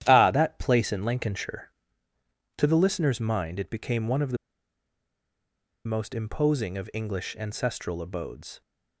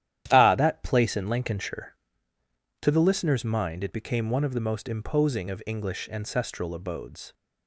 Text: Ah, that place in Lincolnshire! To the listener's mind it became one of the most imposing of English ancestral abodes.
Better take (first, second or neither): second